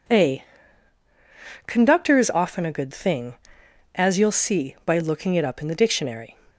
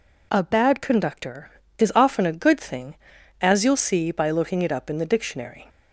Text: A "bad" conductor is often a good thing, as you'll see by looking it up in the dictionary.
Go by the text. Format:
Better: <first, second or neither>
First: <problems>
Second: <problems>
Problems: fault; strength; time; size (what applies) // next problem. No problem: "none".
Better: second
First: skips "bad"; at 1.0 s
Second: none